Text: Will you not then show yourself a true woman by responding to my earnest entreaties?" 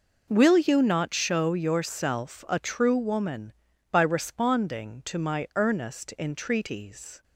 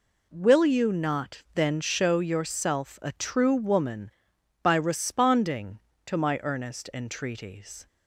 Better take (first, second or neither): second